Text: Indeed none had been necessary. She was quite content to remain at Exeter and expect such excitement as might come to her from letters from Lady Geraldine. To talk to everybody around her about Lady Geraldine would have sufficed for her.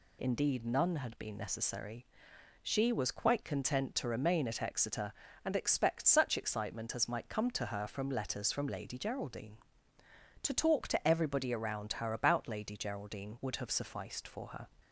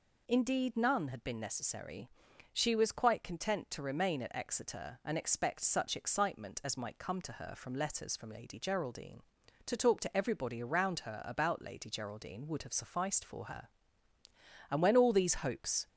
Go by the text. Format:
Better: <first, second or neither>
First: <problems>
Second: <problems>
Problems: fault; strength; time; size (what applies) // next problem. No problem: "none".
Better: first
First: none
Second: goes on to say "And when all these hopes"; noticeable; from 14.6 s on; 1.1 s long